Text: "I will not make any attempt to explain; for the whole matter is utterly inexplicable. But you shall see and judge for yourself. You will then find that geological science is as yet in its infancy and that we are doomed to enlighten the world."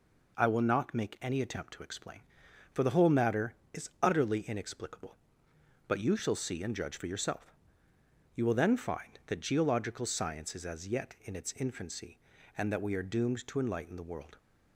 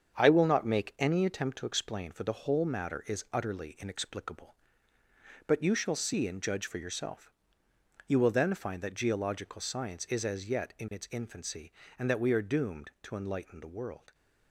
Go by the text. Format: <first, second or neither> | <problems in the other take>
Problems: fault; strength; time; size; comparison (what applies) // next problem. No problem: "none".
first | gets quieter; throughout; 6.5 dB